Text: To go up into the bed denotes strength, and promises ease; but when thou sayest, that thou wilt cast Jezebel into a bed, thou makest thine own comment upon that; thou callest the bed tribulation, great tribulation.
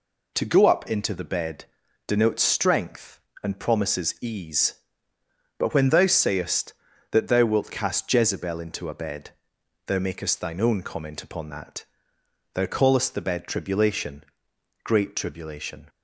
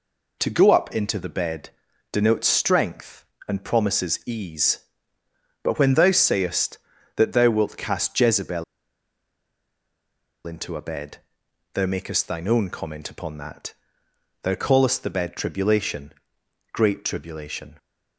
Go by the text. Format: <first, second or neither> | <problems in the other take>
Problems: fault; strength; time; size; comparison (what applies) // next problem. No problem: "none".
first | pauses between "bed" and "denotes"; at 1.7 s; 0.42 s long; also in the first // pauses between "Jezebel" and "into"; strong; at 8.6 s; 1.8 s long